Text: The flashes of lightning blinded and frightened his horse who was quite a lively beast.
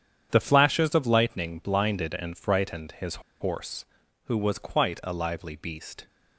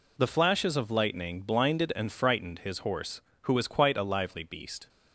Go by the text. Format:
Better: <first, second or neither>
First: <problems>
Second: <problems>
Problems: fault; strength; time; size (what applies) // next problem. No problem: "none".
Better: second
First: starts louder than the rest; strong; until 1.3 s; 8.5 dB // pauses between "his" and "horse"; slight; at 3.1 s; 0.28 s long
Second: none